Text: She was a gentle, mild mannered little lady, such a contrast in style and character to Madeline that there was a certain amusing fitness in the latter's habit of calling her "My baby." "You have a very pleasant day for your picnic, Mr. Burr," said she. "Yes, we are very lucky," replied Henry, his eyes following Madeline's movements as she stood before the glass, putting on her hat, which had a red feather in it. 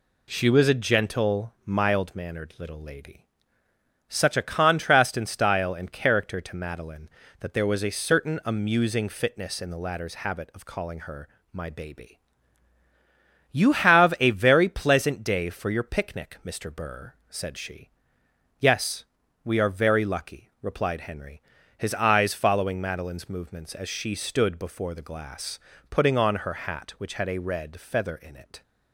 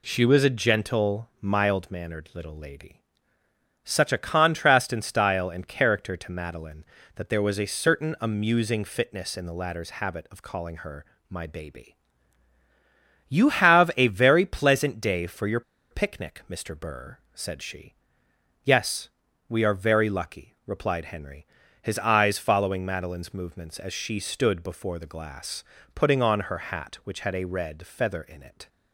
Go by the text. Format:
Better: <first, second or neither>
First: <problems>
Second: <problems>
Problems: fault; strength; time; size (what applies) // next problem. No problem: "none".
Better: first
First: pauses between "her" and "My"; slight; at 11.2 s; 0.24 s long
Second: pauses between "her" and "My"; slight; at 11.0 s; 0.24 s long // pauses between "your" and "picnic"; slight; at 15.6 s; 0.30 s long